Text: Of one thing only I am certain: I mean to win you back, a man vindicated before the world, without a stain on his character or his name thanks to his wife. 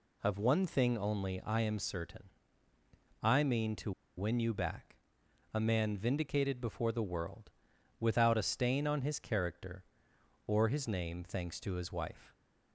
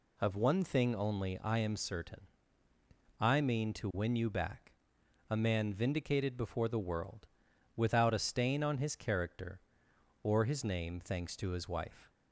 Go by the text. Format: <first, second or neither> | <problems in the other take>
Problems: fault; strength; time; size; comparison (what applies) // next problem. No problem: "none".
second | pauses between "to" and "win"; slight; at 3.9 s; 0.26 s long